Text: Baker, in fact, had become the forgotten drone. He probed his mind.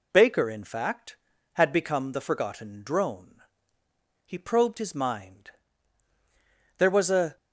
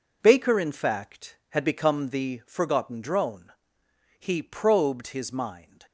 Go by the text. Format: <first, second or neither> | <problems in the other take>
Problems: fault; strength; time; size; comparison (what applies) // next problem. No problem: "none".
second | goes on to say "There was a"; from 6.7 s on; 0.58 s long